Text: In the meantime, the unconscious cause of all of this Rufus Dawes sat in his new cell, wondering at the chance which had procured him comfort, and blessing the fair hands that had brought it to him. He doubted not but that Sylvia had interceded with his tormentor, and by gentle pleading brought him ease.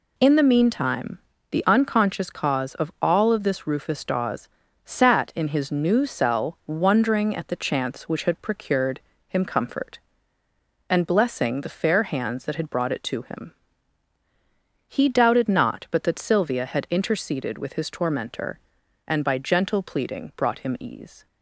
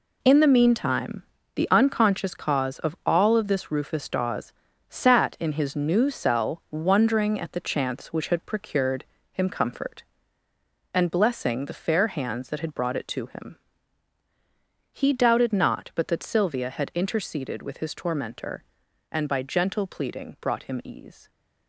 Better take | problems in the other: first | gets quieter; strong; throughout; 9 dB // pauses between "Dawes" and "sat"; slight; at 4.5 s; 0.36 s long; slight in the first // pauses between "procured" and "him"; slight; at 9.0 s; 0.26 s long; slight in the first

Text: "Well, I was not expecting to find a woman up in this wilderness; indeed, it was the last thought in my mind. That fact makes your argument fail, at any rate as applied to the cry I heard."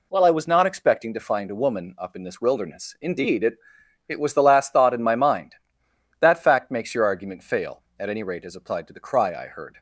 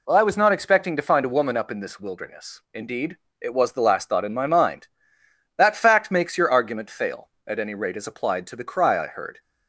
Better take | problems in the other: second | says "it" twice; at 4.0 s

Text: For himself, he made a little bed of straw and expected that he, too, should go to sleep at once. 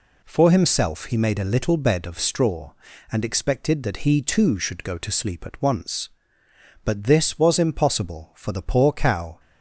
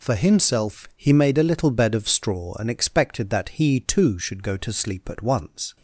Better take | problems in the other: second | goes on to say "But this was impossible for the poor cow"; strong; from 6.8 s on; 2.5 s long

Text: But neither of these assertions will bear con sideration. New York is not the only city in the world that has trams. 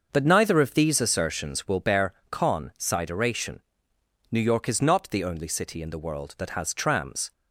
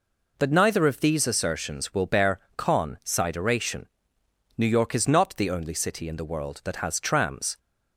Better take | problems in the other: second | starts louder than the rest; until 1.8 s; 6.5 dB // pauses between "bear" and "con"; slight; at 2.1 s; 0.16 s long; slight in the second

